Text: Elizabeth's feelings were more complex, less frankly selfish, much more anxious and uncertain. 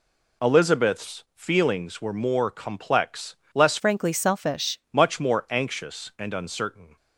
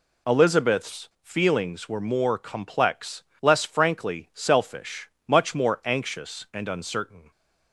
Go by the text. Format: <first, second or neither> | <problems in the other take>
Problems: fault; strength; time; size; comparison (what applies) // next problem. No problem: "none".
second | changes voice from "frankly" to "selfish"; from 3.7 to 4.7 s; 1.0 s long